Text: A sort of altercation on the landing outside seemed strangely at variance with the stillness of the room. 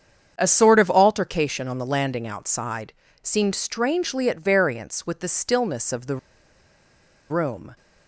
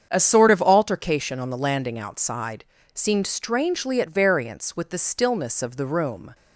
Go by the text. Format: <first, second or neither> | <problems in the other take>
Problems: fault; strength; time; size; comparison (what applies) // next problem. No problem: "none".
second | starts louder than the rest; strong; until 1.3 s; 7.5 dB; strong in the second // pauses between "outside" and "seemed"; slight; at 2.9 s; 0.28 s long; slight in the second // pauses between "the" and "room"; at 6.1 s; 1.1 s long